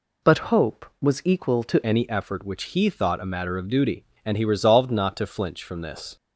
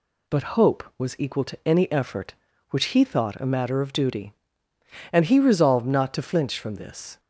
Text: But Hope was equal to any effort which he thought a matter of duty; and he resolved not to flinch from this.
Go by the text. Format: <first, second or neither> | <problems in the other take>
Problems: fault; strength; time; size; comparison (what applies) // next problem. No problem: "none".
second | changes voice at "any"; from 1.8 s on; 4.3 s long